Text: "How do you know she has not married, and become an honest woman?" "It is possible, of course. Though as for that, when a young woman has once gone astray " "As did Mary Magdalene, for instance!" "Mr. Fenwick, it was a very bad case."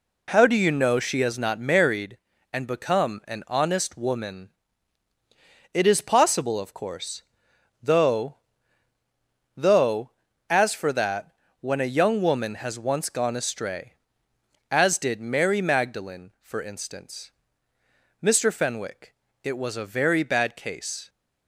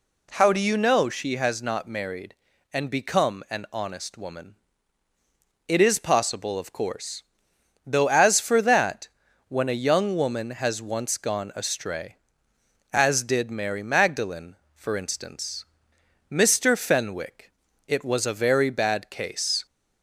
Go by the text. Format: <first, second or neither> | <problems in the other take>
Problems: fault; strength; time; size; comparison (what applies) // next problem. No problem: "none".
second | says "Though" twice; at 9.5 s